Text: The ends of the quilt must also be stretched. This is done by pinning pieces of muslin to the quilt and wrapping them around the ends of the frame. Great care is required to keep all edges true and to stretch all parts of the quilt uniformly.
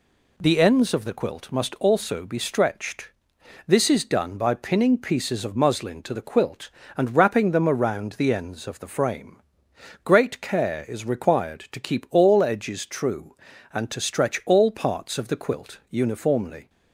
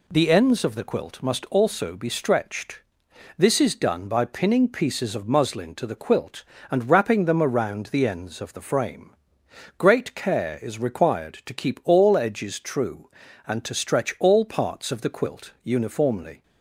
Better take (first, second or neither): neither